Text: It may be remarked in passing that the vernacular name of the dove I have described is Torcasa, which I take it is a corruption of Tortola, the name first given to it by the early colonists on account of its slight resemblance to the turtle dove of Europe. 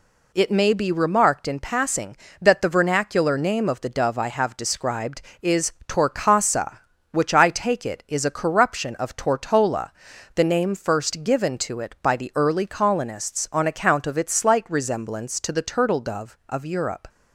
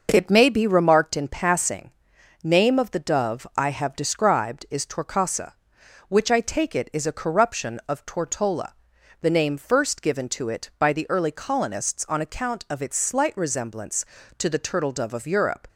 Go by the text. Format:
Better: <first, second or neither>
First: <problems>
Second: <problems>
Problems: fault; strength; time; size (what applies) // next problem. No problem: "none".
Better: first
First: none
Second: skips "that the vernacular"; at 2.1 s